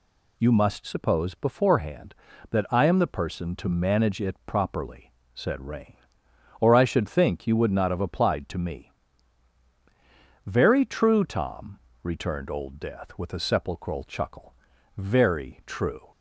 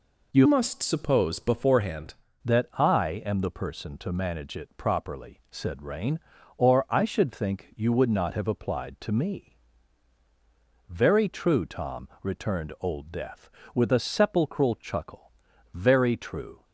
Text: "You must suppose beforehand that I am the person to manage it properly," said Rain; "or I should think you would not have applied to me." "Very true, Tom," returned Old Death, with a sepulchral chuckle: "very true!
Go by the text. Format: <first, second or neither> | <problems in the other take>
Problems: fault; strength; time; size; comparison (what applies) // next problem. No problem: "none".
first | changes voice from "must" to "beforehand"; from 0.4 to 2.1 s; 1.7 s long